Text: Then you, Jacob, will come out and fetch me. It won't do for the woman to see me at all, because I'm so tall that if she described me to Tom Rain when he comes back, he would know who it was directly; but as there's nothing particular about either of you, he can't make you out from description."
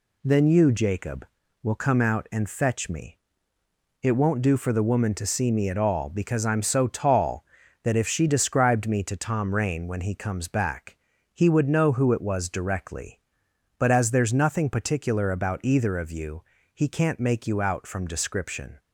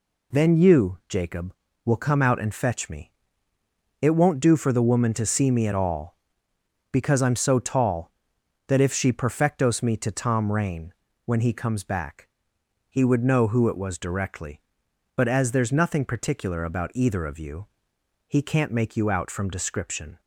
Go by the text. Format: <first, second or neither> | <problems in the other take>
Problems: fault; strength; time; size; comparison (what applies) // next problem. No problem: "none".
first | says "perfectos" for "described"; at 9.1 s // pauses between "Rain" and "when"; slight; at 10.9 s; 0.32 s long